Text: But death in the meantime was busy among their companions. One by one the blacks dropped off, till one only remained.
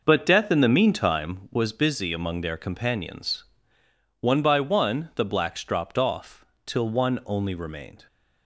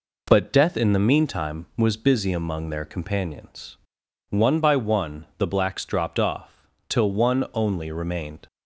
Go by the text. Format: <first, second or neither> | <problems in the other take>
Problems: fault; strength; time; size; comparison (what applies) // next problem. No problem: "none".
second | starts louder than the rest; noticeable; until 1.5 s; 5.5 dB